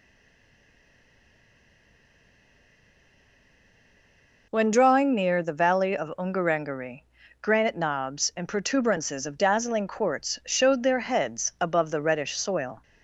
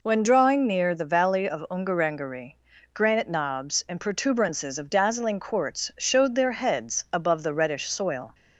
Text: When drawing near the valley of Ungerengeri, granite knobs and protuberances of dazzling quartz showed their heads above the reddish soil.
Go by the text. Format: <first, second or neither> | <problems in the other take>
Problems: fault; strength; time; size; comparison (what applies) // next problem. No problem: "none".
second | stays silent before the first word; strong; until 4.5 s; 4.5 s long